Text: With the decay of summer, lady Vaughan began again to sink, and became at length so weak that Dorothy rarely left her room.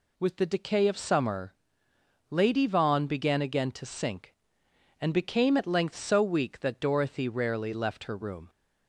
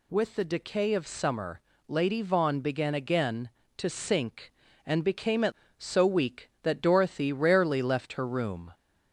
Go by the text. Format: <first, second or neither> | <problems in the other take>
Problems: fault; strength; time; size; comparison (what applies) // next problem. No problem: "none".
first | skips "length"; at 5.6 s